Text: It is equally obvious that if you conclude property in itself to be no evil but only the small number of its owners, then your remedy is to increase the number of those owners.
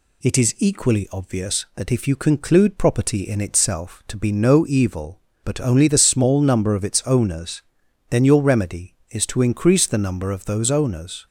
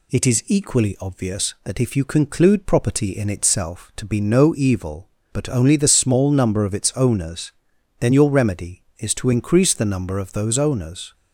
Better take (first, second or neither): neither